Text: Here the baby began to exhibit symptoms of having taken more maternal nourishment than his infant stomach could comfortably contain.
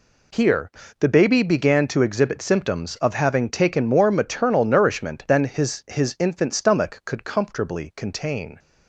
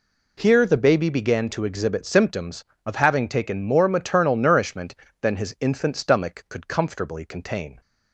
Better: second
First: pauses between "Here" and "the"; slight; at 0.7 s; 0.26 s long // says "his" twice; at 5.8 s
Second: none

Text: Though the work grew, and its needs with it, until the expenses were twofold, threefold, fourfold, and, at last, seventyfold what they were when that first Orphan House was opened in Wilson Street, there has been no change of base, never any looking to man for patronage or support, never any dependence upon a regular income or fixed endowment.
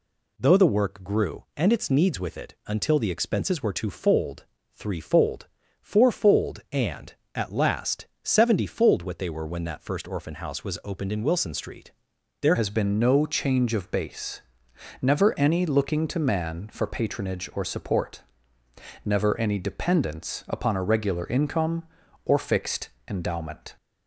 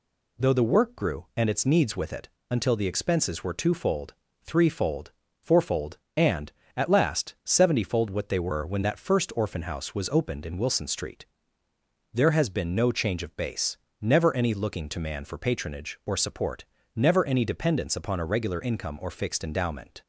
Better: second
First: changes voice at "has"; from 12.5 s on; 11.2 s long // pauses between "fixed" and "endowment"; slight; at 22.8 s; 0.18 s long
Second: none

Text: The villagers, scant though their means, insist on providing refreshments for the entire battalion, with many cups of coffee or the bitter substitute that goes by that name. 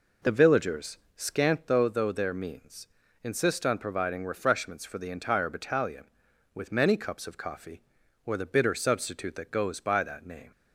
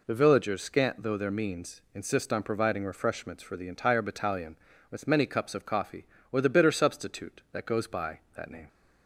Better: second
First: says "though" twice; at 1.8 s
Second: none

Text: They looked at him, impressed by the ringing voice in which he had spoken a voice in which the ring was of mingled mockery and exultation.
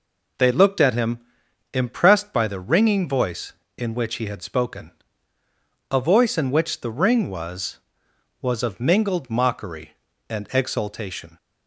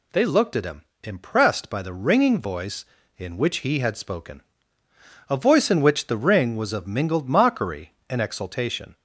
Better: second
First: pauses between "spoken" and "a"; at 4.9 s; 1.0 s long // says "was" twice; at 8.4 s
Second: pauses between "spoken" and "a"; noticeable; at 4.4 s; 0.90 s long

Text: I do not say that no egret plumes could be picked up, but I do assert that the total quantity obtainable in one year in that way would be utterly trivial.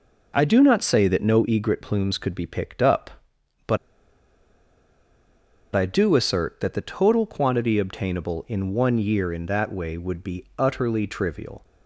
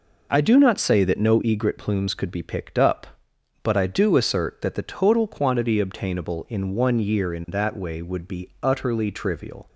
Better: second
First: pauses between "but" and "I"; strong; at 3.7 s; 1.9 s long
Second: none

